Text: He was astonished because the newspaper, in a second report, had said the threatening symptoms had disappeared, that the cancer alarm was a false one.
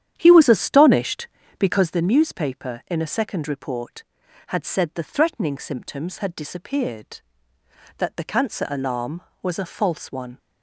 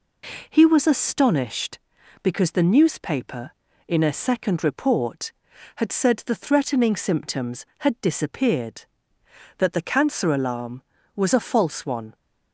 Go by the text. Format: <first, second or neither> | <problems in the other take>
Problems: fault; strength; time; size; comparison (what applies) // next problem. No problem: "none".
second | starts louder than the rest; strong; until 2.0 s; 10 dB